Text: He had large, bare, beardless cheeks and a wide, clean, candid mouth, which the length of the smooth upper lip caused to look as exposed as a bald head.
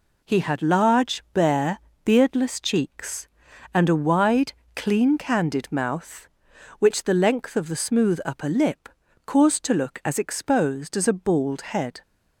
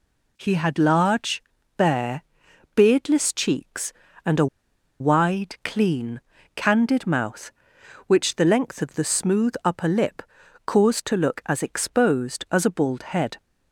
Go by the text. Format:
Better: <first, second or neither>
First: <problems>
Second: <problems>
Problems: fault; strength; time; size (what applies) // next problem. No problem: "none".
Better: first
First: pauses between "lip" and "caused"; at 8.8 s; 0.38 s long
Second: pauses between "a" and "wide"; noticeable; at 4.4 s; 0.53 s long // pauses between "lip" and "caused"; at 10.2 s; 0.44 s long